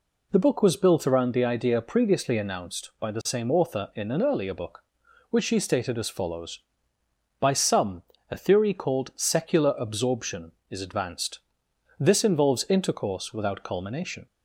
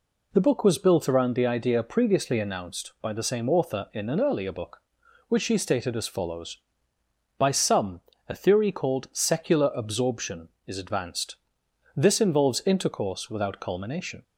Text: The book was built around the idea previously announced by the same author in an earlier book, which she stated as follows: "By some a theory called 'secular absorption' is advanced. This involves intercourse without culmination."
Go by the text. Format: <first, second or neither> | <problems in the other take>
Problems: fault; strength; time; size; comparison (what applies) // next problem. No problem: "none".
neither | pauses between "some" and "a"; slight; the same in both